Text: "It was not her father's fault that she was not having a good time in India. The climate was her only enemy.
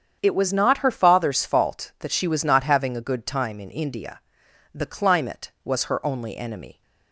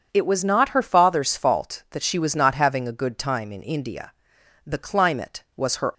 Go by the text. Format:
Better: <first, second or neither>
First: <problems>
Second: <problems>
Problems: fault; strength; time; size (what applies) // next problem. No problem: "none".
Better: first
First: starts louder than the rest; strong; until 1.2 s; 8 dB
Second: starts louder than the rest; strong; until 1.1 s; 7 dB // stops before "only enemy"; at 5.9 s